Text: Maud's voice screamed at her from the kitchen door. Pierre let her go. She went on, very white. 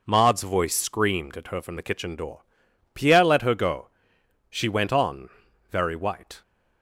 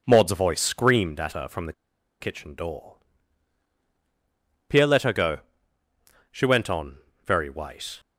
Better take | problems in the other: first | pauses between "the" and "kitchen"; noticeable; at 1.7 s; 0.48 s long

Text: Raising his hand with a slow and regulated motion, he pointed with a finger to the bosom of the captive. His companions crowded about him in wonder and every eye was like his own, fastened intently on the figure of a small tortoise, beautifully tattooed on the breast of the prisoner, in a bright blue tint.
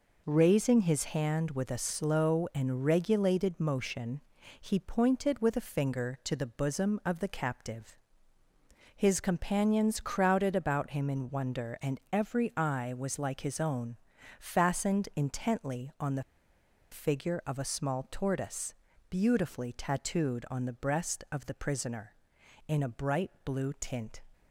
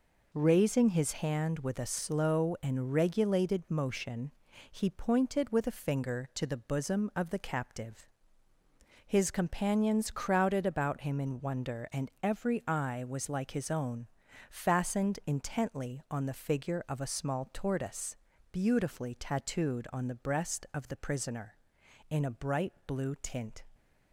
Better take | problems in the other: second | pauses between "the" and "figure"; noticeable; at 16.2 s; 0.69 s long

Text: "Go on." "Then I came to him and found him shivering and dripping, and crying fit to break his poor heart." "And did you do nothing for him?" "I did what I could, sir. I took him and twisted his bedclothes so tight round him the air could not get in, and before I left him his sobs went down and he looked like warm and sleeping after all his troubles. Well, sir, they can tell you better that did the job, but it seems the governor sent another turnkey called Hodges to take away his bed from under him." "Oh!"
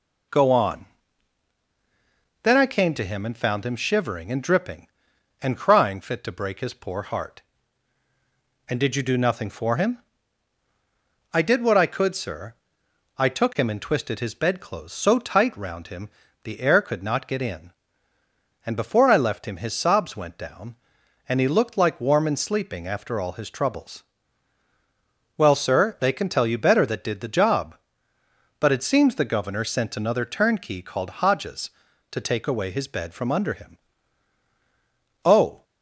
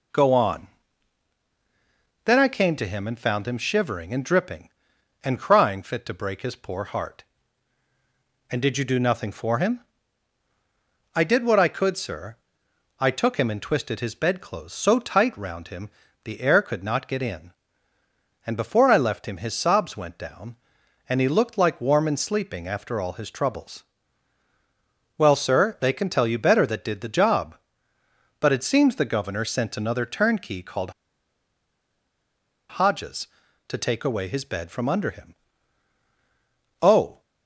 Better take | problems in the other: first | pauses between "him" and "the"; slight; at 15.8 s; 0.36 s long; slight in the first // pauses between "called" and "Hodges"; strong; at 30.9 s; 1.7 s long

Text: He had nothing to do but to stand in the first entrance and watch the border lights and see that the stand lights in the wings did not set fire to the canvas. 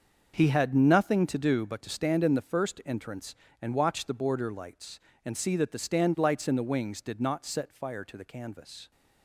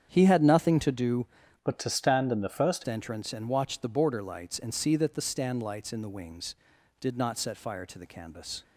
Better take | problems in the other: first | starts louder than the rest; strong; until 1.1 s; 8 dB; also in the first // changes voice from "but" to "first"; from 1.6 to 2.8 s; 1.2 s long

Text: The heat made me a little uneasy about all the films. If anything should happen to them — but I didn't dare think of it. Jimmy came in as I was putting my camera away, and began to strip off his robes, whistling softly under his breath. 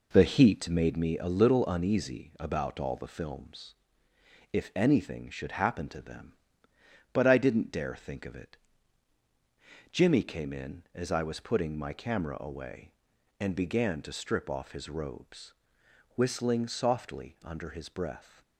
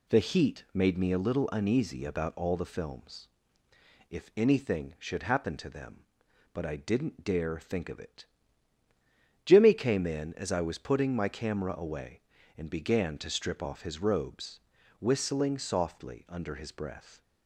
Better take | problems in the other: second | starts louder than the rest; noticeable; until 1.0 s; 4 dB

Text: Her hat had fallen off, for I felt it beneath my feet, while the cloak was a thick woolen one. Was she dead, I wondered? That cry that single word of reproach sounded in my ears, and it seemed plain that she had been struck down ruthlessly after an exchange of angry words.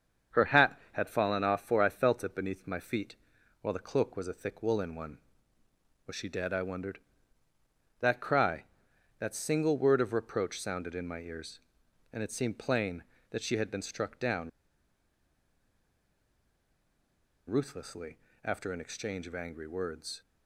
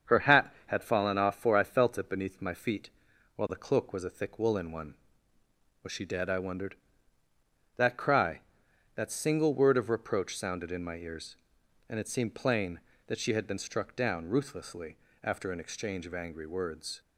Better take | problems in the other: second | starts louder than the rest; until 1.4 s; 7 dB; also in the second // pauses between "down" and "ruthlessly"; strong; at 14.4 s; 2.9 s long // pauses between "ruthlessly" and "after"; slight; at 18.1 s; 0.26 s long; slight in the second

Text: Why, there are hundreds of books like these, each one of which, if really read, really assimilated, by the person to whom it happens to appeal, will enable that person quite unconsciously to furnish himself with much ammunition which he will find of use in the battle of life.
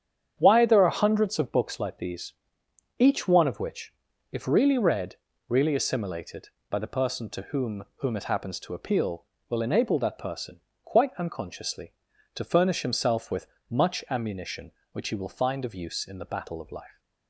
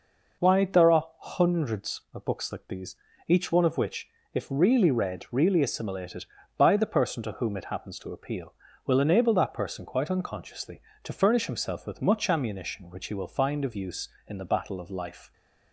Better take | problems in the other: second | starts louder than the rest; strong; until 1.3 s; 8.5 dB // says "whom" twice; at 7.9 s // pauses between "person" and "quite"; slight; at 10.5 s; 0.24 s long // pauses between "with" and "much"; slight; at 13.4 s; 0.22 s long

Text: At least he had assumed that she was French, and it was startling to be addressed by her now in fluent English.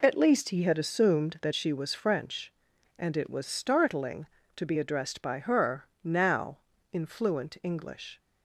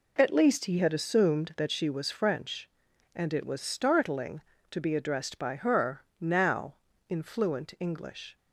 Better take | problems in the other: neither | pauses between "her" and "now"; slight; the same in both

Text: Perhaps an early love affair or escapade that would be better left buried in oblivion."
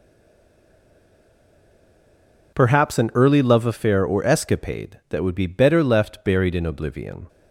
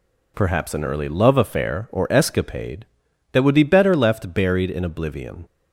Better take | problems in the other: second | stays silent before the first word; strong; until 2.5 s; 2.5 s long

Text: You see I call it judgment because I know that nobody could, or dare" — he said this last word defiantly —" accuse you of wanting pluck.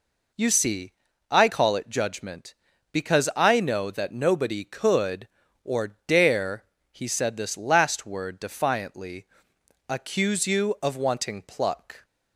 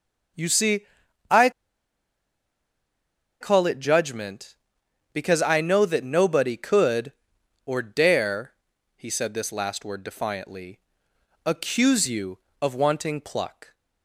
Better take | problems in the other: first | pauses between "see" and "I"; noticeable; at 0.8 s; 0.48 s long; also in the first // pauses between "I" and "call"; strong; at 1.4 s; 1.9 s long

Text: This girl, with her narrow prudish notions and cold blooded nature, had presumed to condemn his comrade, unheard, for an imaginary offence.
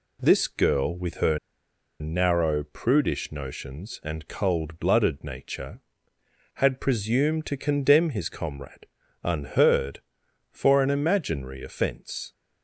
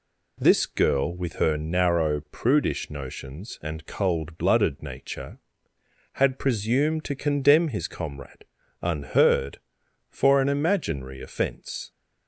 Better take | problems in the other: second | pauses between "her" and "narrow"; noticeable; at 1.3 s; 0.61 s long

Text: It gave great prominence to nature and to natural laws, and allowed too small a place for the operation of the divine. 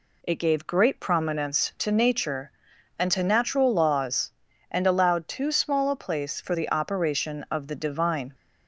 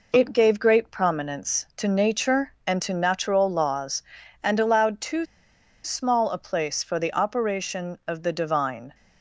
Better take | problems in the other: first | pauses between "too" and "small"; noticeable; at 5.2 s; 0.60 s long

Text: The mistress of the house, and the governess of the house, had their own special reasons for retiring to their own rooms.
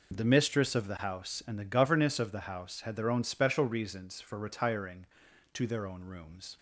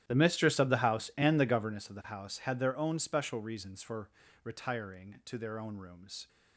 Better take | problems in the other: first | starts louder than the rest; strong; until 1.7 s; 12.5 dB // pauses between "for" and "retiring"; slight; at 4.0 s; 0.36 s long

